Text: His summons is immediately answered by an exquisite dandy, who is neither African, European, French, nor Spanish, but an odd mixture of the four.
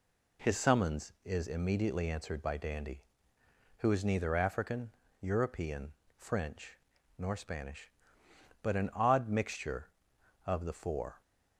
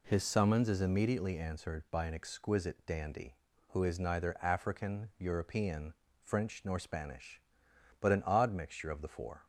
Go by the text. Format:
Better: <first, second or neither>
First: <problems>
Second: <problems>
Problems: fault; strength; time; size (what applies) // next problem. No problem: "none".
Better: second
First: skips "an exquisite"; at 2.5 s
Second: none